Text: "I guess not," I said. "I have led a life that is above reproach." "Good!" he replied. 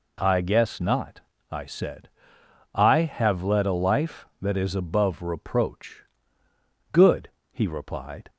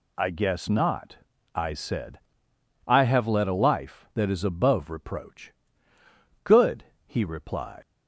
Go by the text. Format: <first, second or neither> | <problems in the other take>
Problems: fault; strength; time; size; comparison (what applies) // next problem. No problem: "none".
first | leaves "replied" unfinished; at 7.8 s; 95 ms